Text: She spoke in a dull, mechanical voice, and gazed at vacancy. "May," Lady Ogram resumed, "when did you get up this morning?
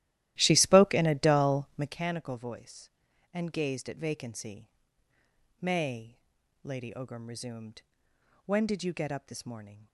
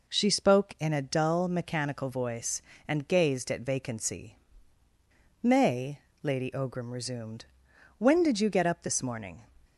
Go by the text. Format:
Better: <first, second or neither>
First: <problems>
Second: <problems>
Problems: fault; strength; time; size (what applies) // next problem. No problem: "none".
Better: second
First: starts louder than the rest; strong; until 2.0 s; 14.5 dB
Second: none